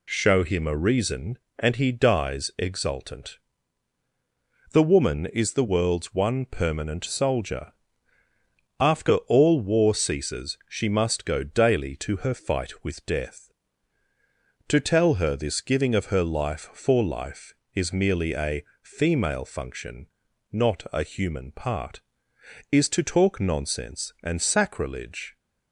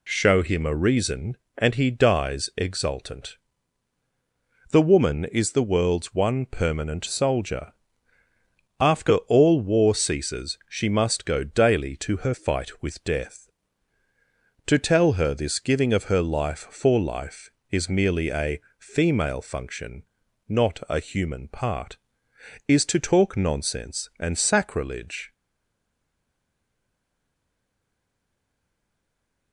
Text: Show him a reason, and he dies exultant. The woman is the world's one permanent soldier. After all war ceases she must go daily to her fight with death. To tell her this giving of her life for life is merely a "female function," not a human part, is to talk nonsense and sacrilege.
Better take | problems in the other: first | pauses between "a" and "female"; slight; at 18.5 s; 0.18 s long; slight in the first // stays silent after the last word; strong; from 25.3 s on; 4.2 s long

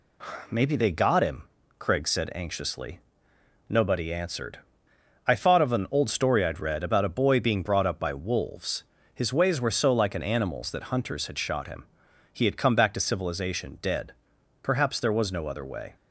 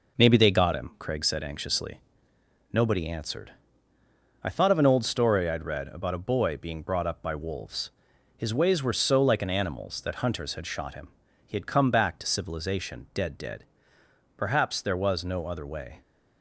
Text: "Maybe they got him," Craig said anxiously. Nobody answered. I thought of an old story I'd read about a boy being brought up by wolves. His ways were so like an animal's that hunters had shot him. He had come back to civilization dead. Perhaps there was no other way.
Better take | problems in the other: first | says "dead" twice; at 13.3 s

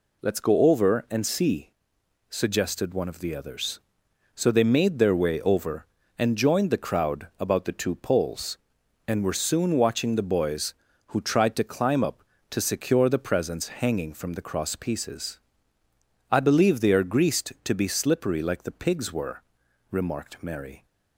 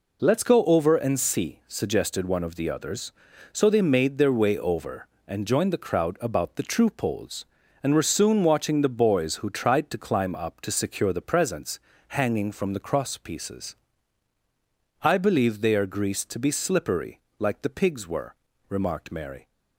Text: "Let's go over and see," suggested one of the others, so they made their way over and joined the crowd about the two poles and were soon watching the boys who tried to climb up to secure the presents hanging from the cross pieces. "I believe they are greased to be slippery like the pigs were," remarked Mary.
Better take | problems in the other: first | says "true" for "two"; at 6.6 s // pauses between "presents" and "hanging"; slight; at 11.7 s; 0.30 s long // pauses between "slippery" and "like"; slight; at 17.1 s; 0.18 s long

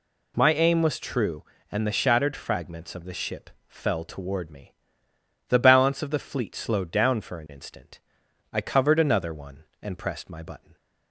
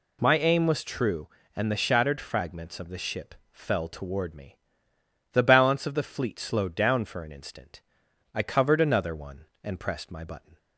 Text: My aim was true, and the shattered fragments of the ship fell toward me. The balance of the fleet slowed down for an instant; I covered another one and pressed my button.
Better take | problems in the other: neither | pauses between "ship" and "fell"; slight; the same in both

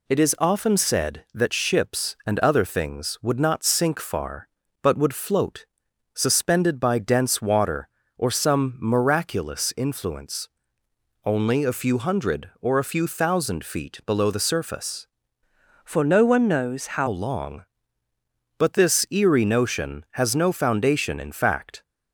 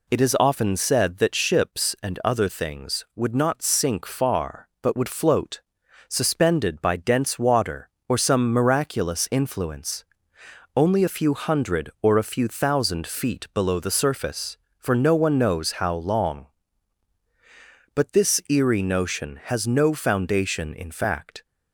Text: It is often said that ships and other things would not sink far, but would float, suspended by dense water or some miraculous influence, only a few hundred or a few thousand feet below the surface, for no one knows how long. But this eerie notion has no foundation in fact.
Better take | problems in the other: second | changes voice from "for" to "how"; from 15.8 to 17.0 s; 1.2 s long

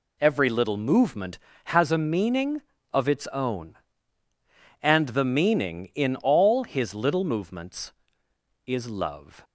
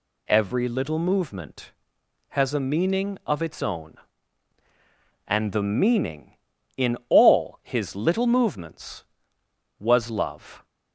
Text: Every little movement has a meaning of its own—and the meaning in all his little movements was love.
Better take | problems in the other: second | says "is" for "was"; at 8.6 s

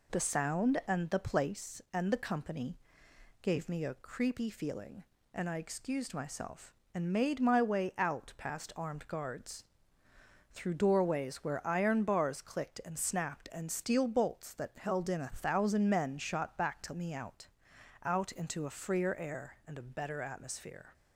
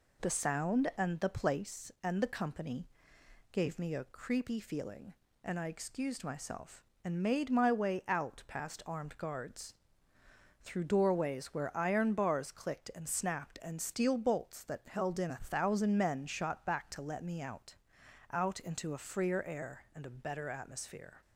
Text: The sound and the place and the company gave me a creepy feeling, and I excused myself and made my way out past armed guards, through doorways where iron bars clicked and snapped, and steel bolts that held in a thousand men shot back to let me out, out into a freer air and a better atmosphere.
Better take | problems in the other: second | pauses between "company" and "gave"; noticeable; at 2.7 s; 0.66 s long; noticeable in the second // skips "let"; at 16.9 s

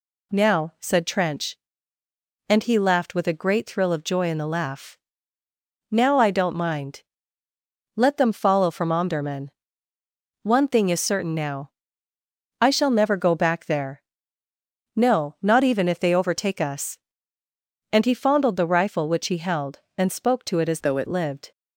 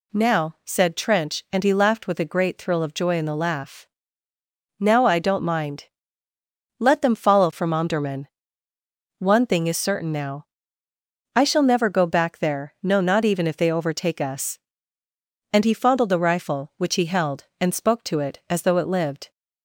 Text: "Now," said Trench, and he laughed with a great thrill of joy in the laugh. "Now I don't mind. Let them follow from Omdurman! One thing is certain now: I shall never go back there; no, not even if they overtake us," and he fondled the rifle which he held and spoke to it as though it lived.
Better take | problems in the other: second | changes voice from "though" to "it"; from 20.8 to 21.0 s; 0.2 s long

